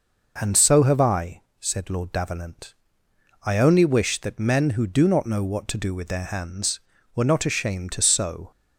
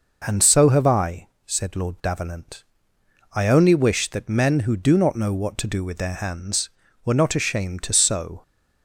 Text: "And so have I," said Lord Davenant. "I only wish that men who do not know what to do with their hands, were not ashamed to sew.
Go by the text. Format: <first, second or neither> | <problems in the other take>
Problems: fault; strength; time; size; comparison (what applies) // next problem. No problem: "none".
neither | none